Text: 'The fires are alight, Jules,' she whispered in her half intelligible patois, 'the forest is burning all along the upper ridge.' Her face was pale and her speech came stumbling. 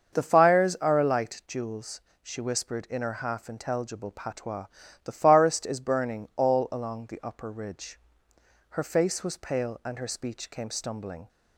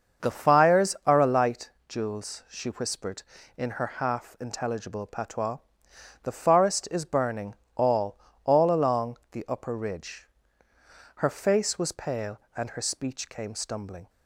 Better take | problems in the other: first | starts louder than the rest; until 1.3 s; 6.5 dB; also in the first // pauses between "burning" and "all"; slight; at 7.5 s; 0.20 s long // says "all" twice; at 8.4 s // pauses between "along" and "the"; slight; at 9.1 s; 0.16 s long

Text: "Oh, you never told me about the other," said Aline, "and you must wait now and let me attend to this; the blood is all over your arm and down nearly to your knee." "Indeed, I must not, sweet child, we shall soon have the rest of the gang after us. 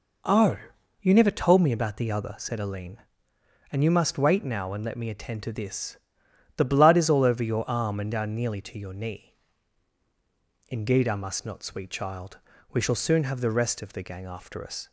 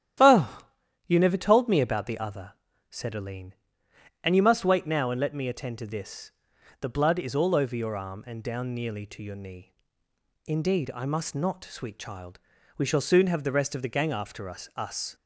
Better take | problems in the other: first | starts louder than the rest; strong; until 1.6 s; 11 dB // says "us" twice; at 14.7 s

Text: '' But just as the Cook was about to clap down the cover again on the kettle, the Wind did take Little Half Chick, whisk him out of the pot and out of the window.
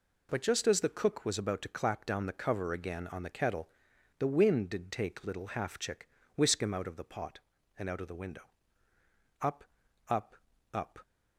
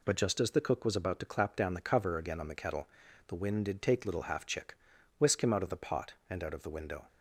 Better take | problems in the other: second | goes on to say "Up up up"; from 9.4 s on; 1.5 s long

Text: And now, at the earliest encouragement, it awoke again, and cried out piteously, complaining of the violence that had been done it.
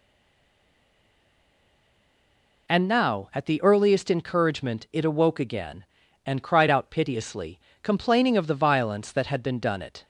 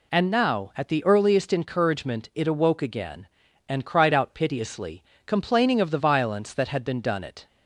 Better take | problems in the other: second | stays silent before the first word; strong; until 2.6 s; 2.6 s long

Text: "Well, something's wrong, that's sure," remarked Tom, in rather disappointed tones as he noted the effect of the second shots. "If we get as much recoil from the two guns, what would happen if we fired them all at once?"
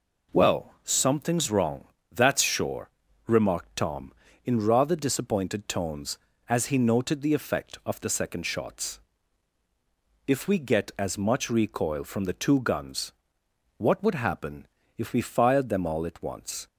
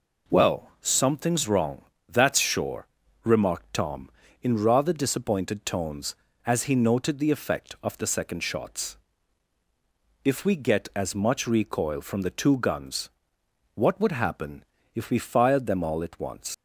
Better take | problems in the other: first | pauses between "happen" and "if"; slight; at 14.6 s; 0.32 s long; slight in the first // leaves "once" unfinished; at 16.5 s; 95 ms

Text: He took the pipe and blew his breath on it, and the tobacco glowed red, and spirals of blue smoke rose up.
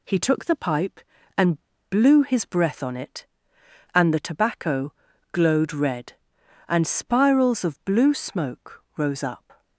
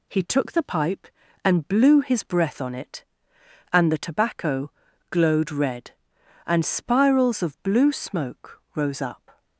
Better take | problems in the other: second | pauses between "and" and "blew"; slight; at 1.5 s; 0.31 s long // pauses between "tobacco" and "glowed"; at 4.9 s; 0.38 s long; also in the second

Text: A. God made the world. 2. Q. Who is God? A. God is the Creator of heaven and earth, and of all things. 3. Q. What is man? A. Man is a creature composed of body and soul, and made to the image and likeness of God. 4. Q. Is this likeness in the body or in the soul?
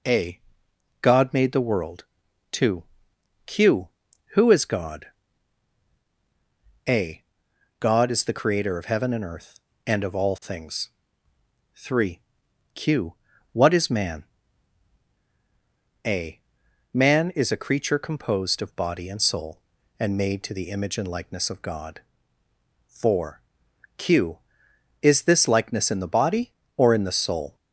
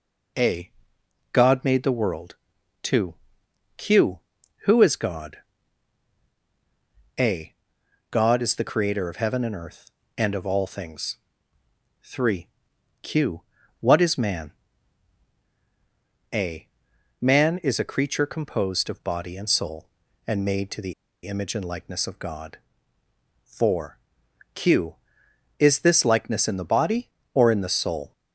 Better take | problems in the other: first | pauses between "the" and "image"; slight; at 20.9 s; 0.32 s long

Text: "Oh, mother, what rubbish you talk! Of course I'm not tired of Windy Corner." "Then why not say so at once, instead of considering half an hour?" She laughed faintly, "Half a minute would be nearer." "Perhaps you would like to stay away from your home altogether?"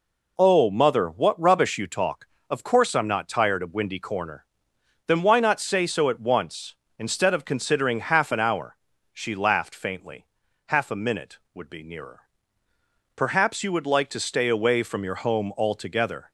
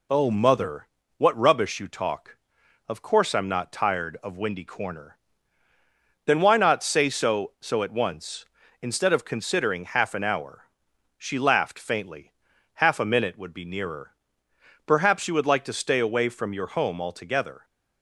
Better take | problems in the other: first | says "so" twice; at 7.5 s

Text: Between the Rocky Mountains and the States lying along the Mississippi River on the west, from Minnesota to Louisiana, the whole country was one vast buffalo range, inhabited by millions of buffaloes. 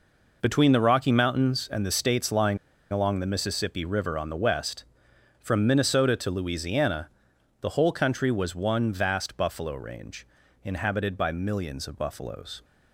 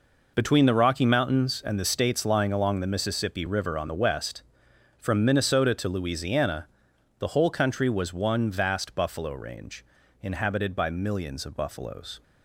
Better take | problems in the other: second | pauses between "lying" and "along"; slight; at 2.5 s; 0.33 s long

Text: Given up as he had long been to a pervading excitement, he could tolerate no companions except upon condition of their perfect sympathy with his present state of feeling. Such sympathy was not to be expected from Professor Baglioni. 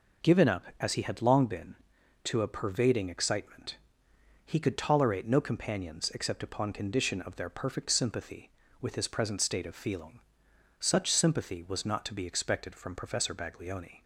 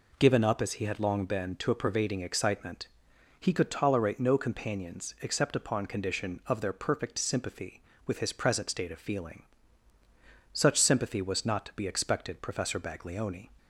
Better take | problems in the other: first | skips "from"; at 12.4 s

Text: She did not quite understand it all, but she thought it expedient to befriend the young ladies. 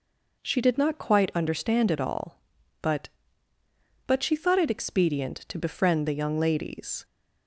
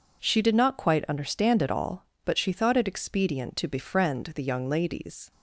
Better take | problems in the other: second | says "but" twice; at 4.0 s

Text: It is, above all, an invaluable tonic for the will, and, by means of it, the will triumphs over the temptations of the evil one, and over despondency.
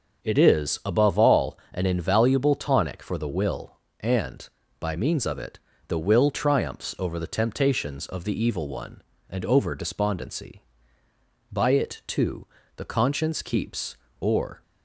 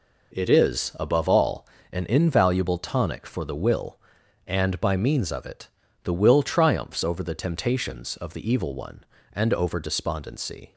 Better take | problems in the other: second | starts louder than the rest; until 1.2 s; 6.5 dB // goes on to say "By it too the conscience keeps or"; strong; from 11.5 s on; 3.1 s long

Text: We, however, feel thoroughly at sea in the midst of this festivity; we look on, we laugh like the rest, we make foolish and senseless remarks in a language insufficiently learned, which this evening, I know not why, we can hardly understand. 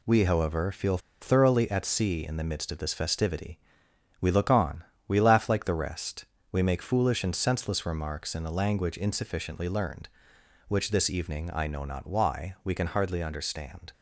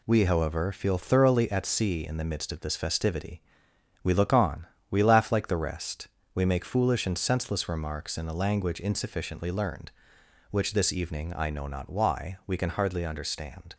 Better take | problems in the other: second | pauses between "feel" and "thoroughly"; slight; at 0.9 s; 0.23 s long

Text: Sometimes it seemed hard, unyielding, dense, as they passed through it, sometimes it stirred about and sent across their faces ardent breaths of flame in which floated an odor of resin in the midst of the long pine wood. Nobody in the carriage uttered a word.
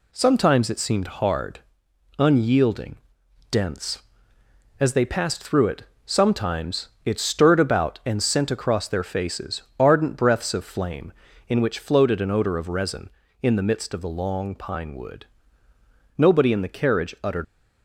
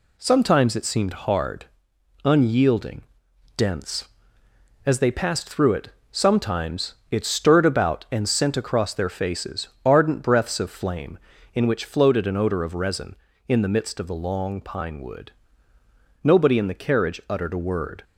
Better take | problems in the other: second | pauses between "sometimes" and "it"; slight; at 6.8 s; 0.16 s long; slight in the second // pauses between "faces" and "ardent"; slight; at 9.6 s; 0.18 s long; slight in the second // stops before "a word"; at 17.4 s

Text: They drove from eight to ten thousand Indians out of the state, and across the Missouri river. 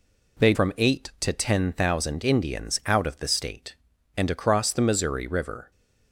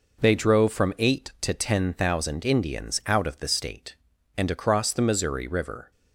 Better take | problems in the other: second | skips "drove"; at 0.5 s

